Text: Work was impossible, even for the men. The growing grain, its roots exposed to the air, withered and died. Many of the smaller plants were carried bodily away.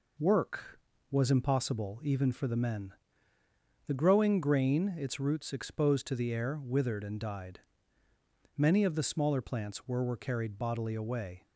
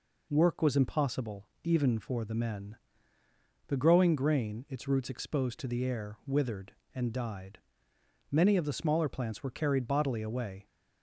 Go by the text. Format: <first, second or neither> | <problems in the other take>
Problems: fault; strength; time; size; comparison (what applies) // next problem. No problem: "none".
second | says "were" twice; at 10.0 s